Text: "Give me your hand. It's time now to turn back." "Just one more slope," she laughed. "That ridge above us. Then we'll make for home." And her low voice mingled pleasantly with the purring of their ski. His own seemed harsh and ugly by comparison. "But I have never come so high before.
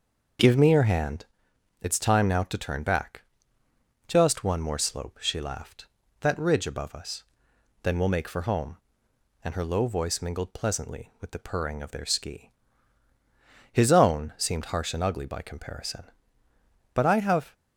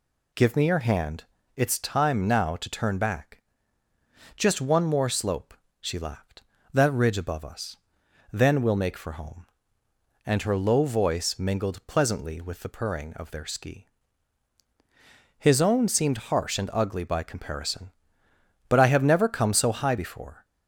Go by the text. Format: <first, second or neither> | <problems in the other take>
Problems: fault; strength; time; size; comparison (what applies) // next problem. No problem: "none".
second | starts louder than the rest; until 1.9 s; 6 dB // stops before "never come so high before"; at 17.5 s